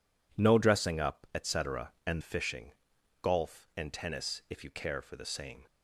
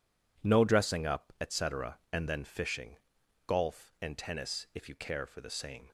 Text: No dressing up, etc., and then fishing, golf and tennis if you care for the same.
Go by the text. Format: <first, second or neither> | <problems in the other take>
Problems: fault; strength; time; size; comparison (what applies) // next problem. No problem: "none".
second | skips "then"; at 2.2 s